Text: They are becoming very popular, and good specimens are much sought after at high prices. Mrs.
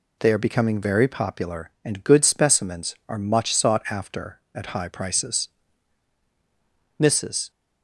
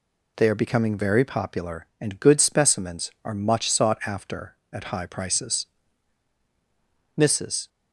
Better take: neither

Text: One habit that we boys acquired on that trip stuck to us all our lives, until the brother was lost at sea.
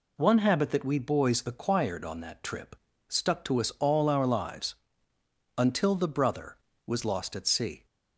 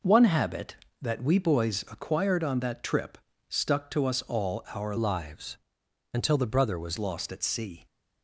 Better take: first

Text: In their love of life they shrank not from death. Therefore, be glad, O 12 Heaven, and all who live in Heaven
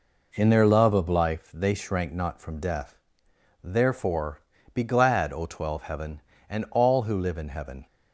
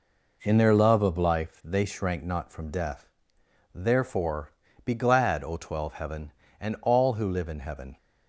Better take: neither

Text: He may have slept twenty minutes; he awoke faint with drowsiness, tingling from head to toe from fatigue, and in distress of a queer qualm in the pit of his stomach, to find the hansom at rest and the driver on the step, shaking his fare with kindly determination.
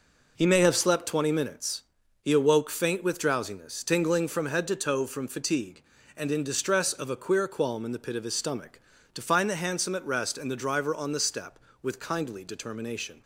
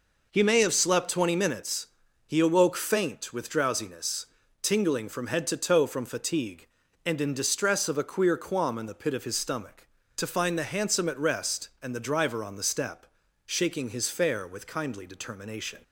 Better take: second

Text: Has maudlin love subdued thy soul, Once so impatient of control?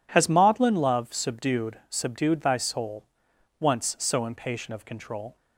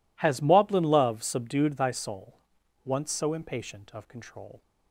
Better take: second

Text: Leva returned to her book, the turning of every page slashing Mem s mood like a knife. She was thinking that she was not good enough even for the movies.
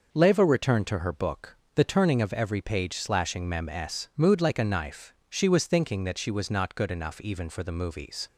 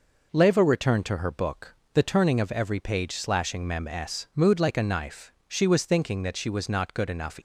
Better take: first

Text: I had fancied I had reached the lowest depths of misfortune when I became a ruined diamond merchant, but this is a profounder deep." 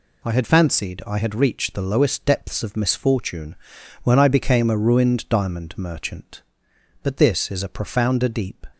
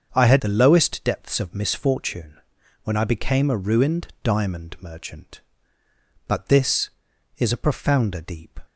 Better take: first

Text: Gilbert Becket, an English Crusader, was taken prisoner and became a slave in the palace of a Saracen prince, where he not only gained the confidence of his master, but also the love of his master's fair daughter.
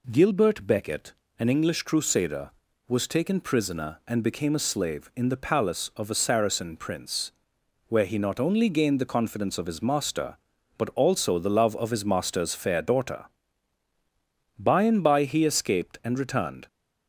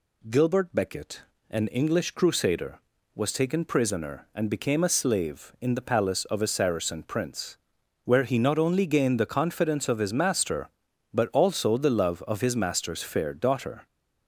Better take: second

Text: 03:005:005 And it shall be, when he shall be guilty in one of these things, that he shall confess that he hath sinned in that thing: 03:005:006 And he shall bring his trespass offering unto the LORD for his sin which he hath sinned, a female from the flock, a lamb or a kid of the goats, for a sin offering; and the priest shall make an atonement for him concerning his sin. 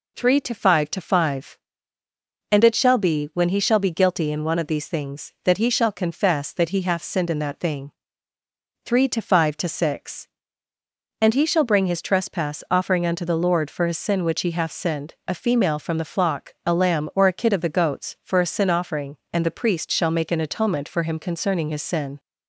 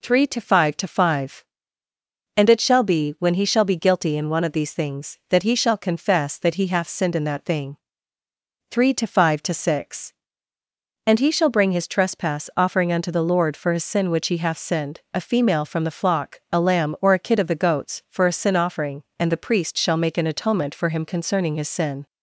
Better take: neither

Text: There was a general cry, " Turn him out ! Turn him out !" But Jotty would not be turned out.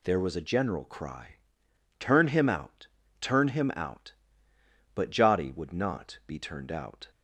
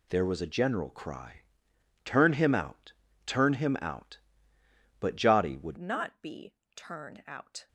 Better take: first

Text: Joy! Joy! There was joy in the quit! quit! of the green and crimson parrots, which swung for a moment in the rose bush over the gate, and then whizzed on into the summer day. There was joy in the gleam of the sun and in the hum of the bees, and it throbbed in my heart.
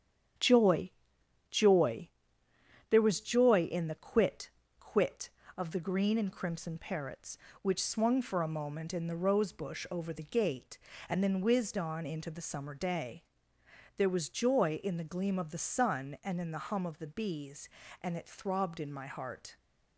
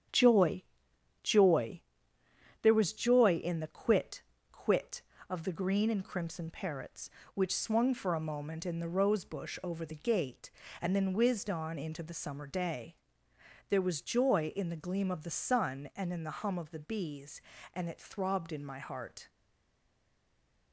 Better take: first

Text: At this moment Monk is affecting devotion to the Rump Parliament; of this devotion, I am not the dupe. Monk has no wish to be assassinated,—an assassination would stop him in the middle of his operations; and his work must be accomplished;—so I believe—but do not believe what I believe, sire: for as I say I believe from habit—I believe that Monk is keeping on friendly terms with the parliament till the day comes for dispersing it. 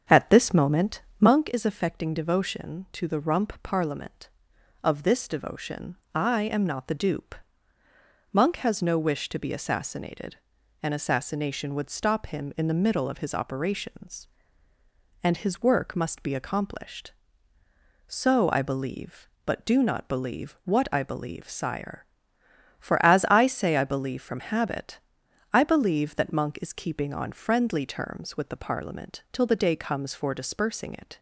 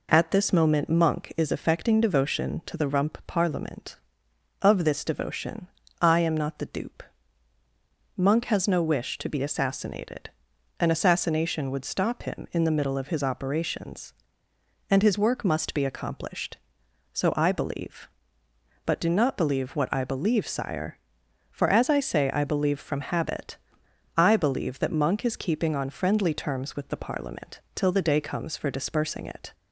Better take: second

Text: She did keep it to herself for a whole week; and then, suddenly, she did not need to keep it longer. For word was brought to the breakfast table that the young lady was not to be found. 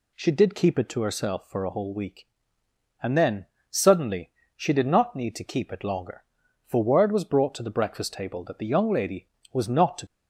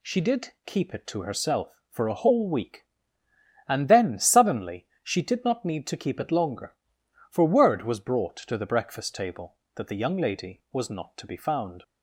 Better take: second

